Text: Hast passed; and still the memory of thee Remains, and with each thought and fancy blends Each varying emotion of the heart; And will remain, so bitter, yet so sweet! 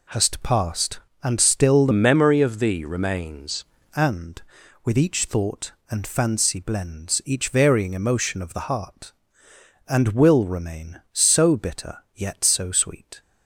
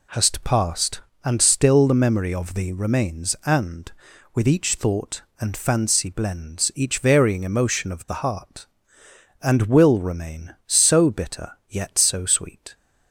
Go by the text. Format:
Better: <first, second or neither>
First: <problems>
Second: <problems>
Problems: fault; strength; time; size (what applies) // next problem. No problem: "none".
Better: second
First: changes voice from "memory" to "Remains"; from 1.9 to 3.6 s; 1.7 s long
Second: none